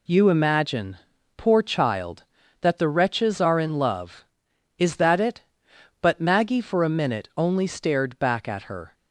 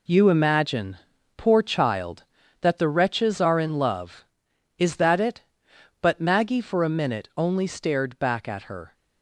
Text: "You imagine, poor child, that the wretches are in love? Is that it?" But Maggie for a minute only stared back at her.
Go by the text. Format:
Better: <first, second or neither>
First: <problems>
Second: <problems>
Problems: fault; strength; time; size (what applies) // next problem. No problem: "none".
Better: first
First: none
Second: gets quieter; strong; throughout; 8 dB